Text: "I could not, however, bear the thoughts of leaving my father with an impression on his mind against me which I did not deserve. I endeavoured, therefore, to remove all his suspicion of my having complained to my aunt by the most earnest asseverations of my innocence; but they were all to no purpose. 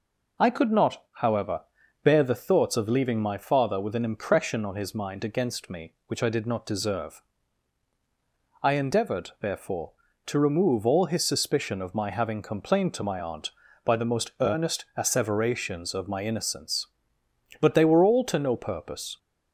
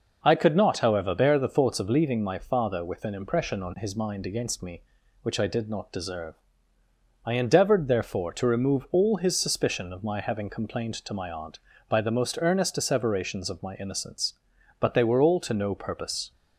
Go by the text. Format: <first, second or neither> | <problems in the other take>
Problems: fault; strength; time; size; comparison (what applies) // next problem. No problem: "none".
neither | none